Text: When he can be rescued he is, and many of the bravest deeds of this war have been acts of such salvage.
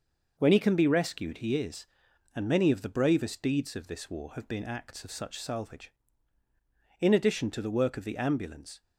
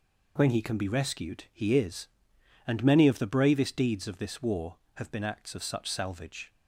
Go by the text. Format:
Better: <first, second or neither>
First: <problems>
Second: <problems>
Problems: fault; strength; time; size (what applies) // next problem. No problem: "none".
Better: second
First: goes on to say "In addition to the work of the ambulance"; strong; from 6.9 s on; 1.8 s long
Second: none